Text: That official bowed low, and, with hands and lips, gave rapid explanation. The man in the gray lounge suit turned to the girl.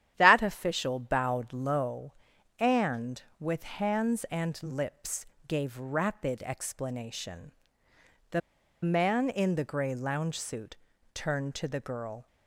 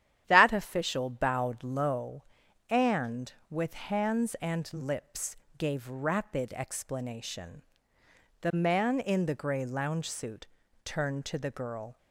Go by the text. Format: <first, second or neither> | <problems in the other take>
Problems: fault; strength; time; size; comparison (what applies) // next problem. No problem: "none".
second | starts louder than the rest; strong; until 1.1 s; 10.5 dB; strong in the second // pauses between "The" and "man"; at 8.4 s; 0.44 s long // pauses between "suit" and "turned"; at 10.7 s; 0.38 s long; also in the second